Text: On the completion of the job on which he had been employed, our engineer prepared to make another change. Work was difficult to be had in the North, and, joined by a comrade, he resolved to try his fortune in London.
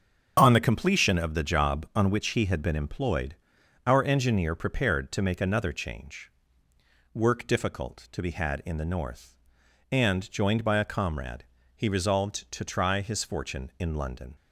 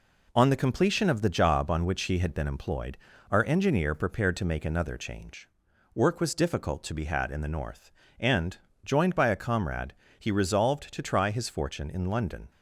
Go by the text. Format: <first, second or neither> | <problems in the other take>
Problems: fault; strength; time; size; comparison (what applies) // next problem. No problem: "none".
second | starts louder than the rest; strong; until 1.3 s; 8 dB // skips "was"; at 7.4 s